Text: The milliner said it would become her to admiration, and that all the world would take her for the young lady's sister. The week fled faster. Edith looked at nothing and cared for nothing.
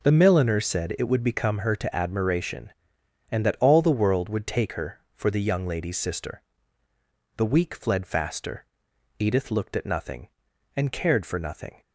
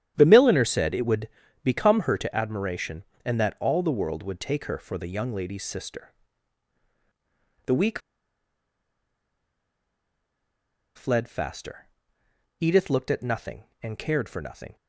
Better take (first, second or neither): first